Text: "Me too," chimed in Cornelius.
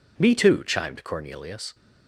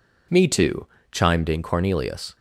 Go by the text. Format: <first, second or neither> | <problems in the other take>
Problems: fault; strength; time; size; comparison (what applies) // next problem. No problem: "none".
second | skips "in"; at 1.0 s